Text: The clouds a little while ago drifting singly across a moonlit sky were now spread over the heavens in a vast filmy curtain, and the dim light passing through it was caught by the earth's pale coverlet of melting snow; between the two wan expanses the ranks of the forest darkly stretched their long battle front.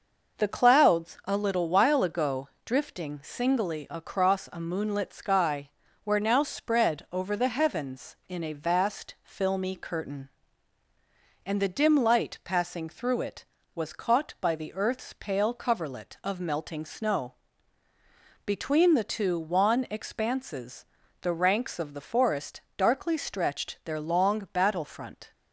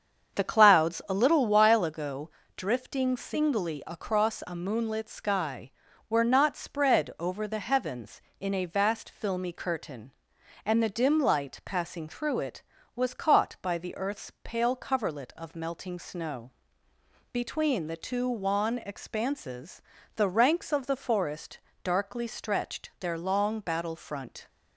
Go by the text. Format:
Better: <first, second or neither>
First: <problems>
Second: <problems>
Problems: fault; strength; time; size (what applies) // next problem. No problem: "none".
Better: first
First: pauses between "ago" and "drifting"; slight; at 2.4 s; 0.16 s long // pauses between "expanses" and "the"; at 20.8 s; 0.38 s long // pauses between "forest" and "darkly"; slight; at 22.5 s; 0.16 s long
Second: starts louder than the rest; strong; until 1.4 s; 7.5 dB // pauses between "ago" and "drifting"; slight; at 2.2 s; 0.28 s long // says "not" for "now"; at 6.2 s // pauses between "expanses" and "the"; slight; at 19.8 s; 0.34 s long // pauses between "forest" and "darkly"; slight; at 21.5 s; 0.24 s long